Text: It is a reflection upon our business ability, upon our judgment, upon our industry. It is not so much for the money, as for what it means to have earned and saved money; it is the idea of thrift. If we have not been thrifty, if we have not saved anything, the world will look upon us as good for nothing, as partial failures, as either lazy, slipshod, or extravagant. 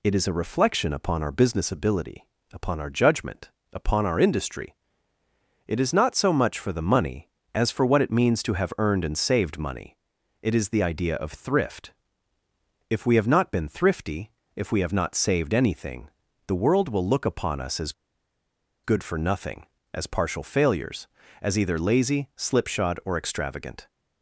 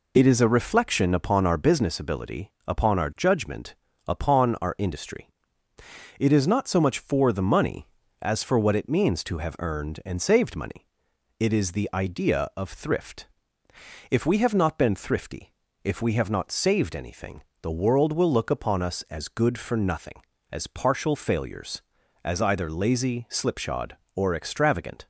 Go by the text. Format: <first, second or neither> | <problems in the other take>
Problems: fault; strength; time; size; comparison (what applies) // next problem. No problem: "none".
second | pauses between "as" and "good"; noticeable; at 17.9 s; 0.92 s long